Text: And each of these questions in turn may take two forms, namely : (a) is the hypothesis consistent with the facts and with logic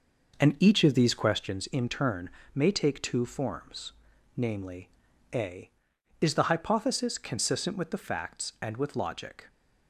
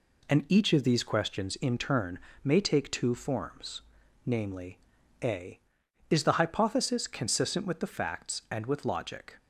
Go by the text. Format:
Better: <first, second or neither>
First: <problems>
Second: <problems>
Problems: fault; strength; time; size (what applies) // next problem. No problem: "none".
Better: second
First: starts louder than the rest; noticeable; until 1.5 s; 5.5 dB // pauses between "turn" and "may"; slight; at 2.2 s; 0.26 s long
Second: pauses between "turn" and "may"; slight; at 2.1 s; 0.26 s long